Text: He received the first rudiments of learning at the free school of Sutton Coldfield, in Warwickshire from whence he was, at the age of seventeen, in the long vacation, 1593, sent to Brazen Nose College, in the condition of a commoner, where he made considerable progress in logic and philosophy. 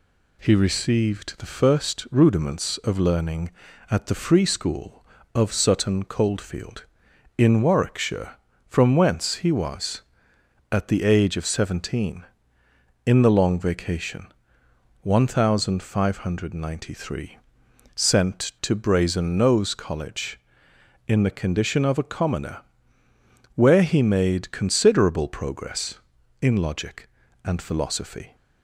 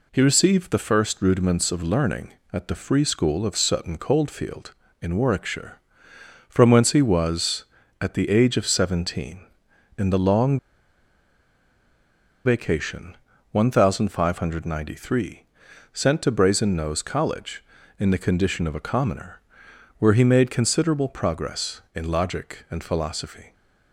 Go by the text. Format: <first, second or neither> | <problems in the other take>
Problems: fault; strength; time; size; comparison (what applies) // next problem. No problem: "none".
first | pauses between "long" and "vacation"; strong; at 10.5 s; 1.8 s long